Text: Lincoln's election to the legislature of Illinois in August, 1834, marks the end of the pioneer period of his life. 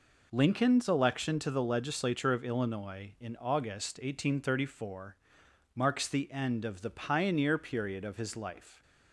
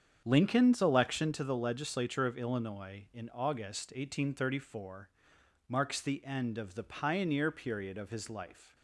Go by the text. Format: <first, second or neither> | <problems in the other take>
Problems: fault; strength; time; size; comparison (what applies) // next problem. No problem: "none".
first | starts louder than the rest; strong; until 1.4 s; 8 dB